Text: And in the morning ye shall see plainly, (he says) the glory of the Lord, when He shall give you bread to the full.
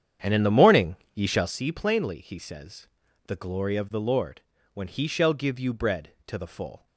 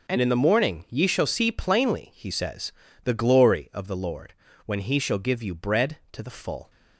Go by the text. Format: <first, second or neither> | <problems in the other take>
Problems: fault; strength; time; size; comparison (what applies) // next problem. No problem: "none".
second | starts louder than the rest; strong; until 1.6 s; 9 dB // pauses between "morning" and "ye"; slight; at 0.9 s; 0.18 s long